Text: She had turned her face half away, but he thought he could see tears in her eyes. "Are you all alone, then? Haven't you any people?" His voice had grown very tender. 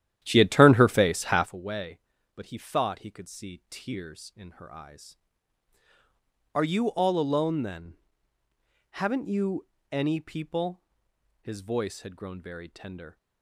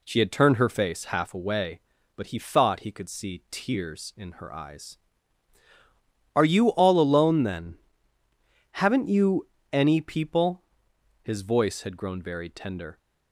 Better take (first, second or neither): second